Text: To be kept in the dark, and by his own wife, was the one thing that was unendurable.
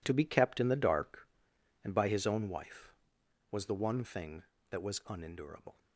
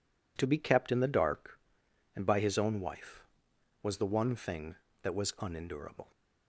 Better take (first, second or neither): second